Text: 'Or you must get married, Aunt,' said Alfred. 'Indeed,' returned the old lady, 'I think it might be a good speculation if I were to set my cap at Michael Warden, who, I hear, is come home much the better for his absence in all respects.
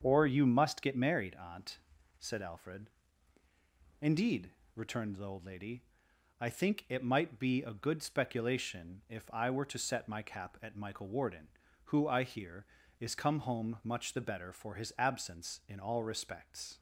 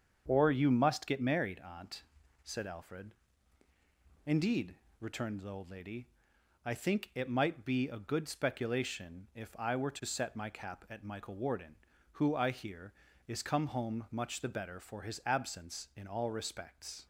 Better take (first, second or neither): neither